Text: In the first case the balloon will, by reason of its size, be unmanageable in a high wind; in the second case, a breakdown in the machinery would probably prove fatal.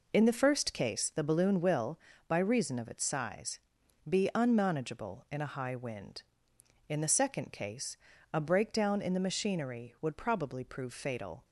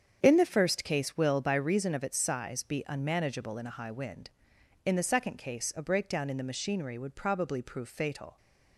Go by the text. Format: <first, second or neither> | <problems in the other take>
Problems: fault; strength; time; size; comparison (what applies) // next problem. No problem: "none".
first | starts louder than the rest; strong; until 1.2 s; 7.5 dB // skips "the balloon"; at 1.1 s